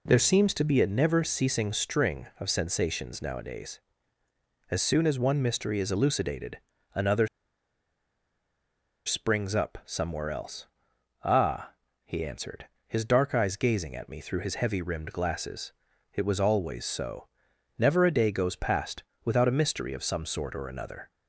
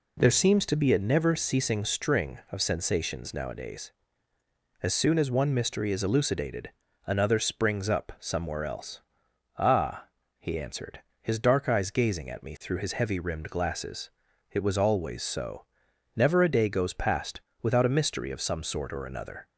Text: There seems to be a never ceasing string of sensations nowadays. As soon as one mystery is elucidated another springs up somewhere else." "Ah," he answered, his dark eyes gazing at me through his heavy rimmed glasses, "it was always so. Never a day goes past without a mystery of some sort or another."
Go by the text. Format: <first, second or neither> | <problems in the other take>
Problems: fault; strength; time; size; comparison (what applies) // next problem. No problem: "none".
second | pauses between "elucidated" and "another"; slight; at 6.5 s; 0.36 s long; slight in the second // pauses between "another" and "springs"; strong; at 7.2 s; 1.7 s long // pauses between "past" and "without"; slight; at 19.0 s; 0.20 s long; slight in the second